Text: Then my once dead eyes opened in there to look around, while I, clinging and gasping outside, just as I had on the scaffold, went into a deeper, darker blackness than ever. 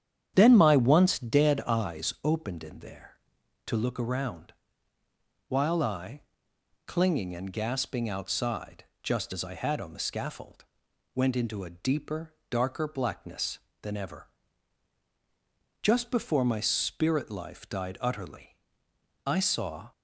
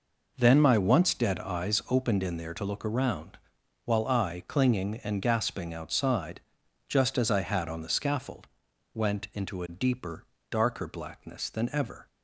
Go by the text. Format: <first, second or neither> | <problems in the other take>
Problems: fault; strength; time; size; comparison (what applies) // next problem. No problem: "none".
second | starts louder than the rest; strong; until 1.3 s; 9 dB // goes on to say "Just before my spirit life died utterly I saw"; strong; from 15.8 s on; 4.1 s long